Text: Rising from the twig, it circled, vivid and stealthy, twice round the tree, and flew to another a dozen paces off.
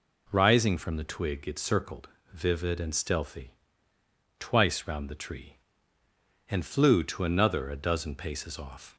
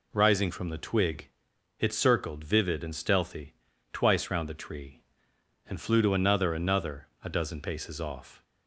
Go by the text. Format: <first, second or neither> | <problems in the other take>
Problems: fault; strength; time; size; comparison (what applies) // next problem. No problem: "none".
first | says "another" twice; at 6.5 s